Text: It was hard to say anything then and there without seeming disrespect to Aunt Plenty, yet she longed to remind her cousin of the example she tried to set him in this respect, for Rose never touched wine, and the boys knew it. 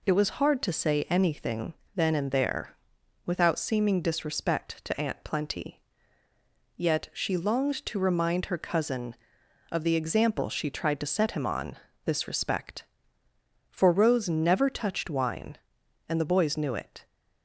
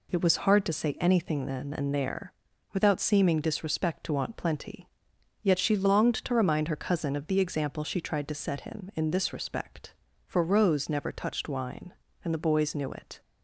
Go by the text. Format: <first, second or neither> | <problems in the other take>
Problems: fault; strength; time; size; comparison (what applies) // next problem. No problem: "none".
second | pauses between "anything" and "then"; slight; at 1.7 s; 0.22 s long // pauses between "there" and "without"; noticeable; at 2.7 s; 0.50 s long; also in the second // says "on" for "in"; at 11.4 s